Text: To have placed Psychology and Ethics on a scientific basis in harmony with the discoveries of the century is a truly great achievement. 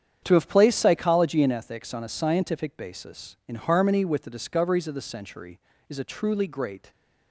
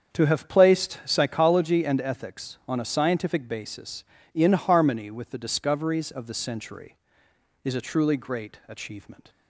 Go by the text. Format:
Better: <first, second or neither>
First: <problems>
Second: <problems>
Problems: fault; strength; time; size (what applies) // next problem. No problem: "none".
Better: second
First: starts louder than the rest; strong; until 1.2 s; 8.5 dB // stops before "achievement"; at 6.9 s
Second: starts louder than the rest; strong; until 1.1 s; 7 dB